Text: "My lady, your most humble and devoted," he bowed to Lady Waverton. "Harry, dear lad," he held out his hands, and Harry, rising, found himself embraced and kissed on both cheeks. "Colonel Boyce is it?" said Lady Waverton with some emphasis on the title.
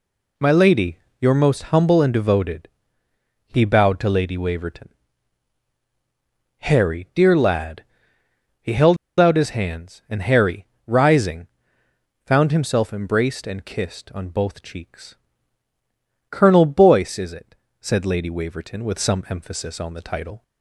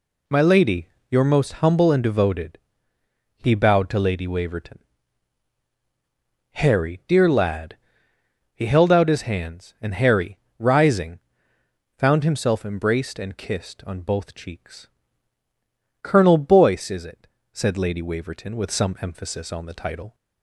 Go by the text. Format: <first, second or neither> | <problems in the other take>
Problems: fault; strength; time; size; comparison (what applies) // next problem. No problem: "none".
second | pauses between "held" and "out"; slight; at 8.9 s; 0.23 s long